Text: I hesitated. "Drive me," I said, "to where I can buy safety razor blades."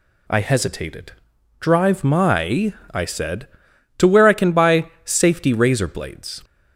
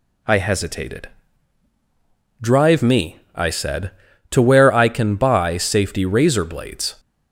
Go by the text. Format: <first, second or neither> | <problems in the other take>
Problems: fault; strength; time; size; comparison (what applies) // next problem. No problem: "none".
second | says "my" for "me"; at 2.0 s // pauses between "buy" and "safety"; slight; at 4.8 s; 0.18 s long